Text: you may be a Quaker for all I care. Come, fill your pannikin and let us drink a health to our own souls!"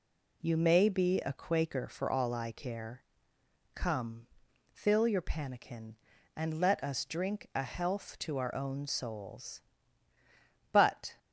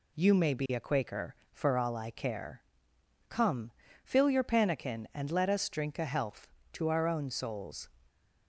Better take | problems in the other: second | goes on to say "But"; slight; from 10.7 s on; 0.46 s long

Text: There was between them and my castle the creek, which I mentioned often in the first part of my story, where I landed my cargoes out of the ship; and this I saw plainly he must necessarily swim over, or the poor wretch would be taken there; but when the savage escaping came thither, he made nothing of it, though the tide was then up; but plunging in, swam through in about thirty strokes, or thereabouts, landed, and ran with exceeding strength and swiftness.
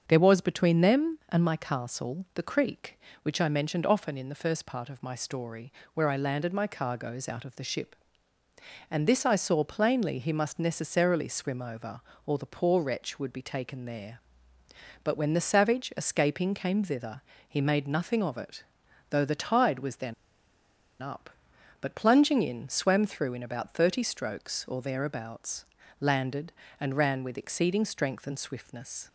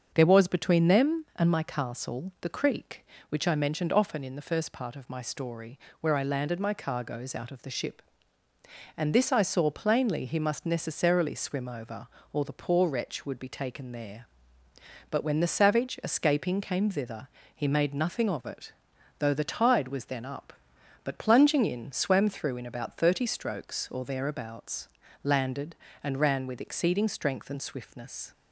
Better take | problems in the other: second | starts louder than the rest; until 1.0 s; 7 dB; also in the second // pauses between "then" and "up"; noticeable; at 20.1 s; 0.87 s long

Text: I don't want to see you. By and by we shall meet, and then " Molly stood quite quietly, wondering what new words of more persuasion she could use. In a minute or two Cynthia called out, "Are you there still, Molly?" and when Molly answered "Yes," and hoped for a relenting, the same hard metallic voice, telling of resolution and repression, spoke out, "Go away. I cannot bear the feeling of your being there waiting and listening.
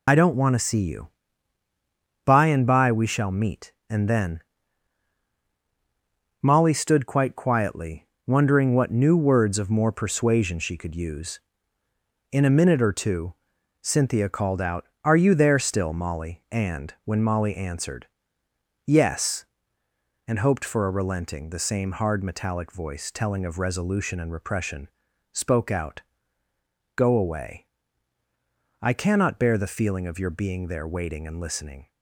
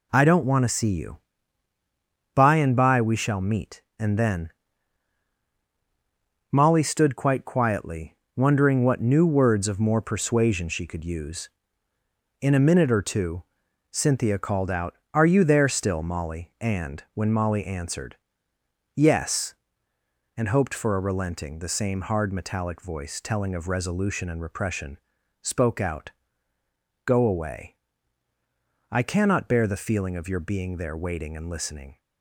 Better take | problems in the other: second | loses the start of "I"; at 0.0 s; 60 ms // pauses between "two" and "Cynthia"; noticeable; at 13.3 s; 0.48 s long; noticeable in the second // pauses between "answered" and "Yes"; noticeable; at 18.0 s; 0.78 s long; noticeable in the second

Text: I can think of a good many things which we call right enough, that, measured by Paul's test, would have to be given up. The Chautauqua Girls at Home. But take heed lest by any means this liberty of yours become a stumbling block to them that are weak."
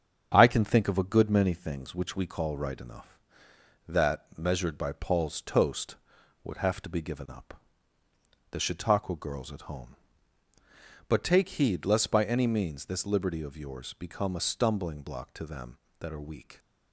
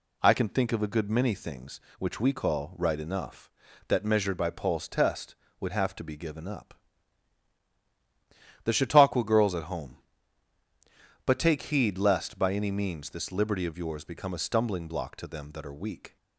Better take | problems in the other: second | starts louder than the rest; strong; until 1.3 s; 7.5 dB // says "toast" for "test"; at 5.4 s

